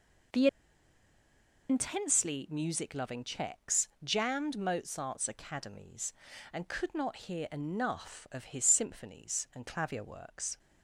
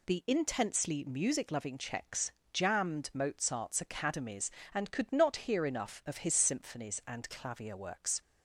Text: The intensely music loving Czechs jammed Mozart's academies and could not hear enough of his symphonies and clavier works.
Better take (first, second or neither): second